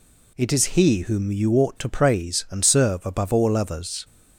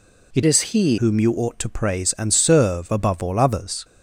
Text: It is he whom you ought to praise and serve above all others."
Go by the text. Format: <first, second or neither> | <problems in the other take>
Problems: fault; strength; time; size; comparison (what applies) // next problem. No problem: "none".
first | changes voice from "is" to "he"; from 0.4 to 0.9 s; 0.5 s long